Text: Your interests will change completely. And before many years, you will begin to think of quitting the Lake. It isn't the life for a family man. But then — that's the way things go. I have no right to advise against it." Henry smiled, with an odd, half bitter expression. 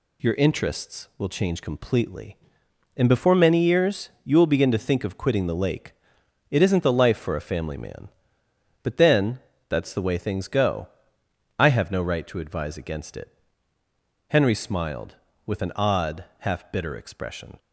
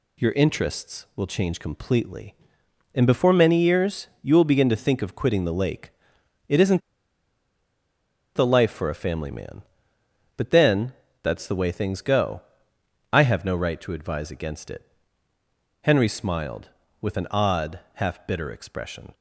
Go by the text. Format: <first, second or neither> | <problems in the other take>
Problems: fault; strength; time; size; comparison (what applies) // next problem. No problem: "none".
first | pauses between "isn't" and "the"; strong; at 6.8 s; 1.5 s long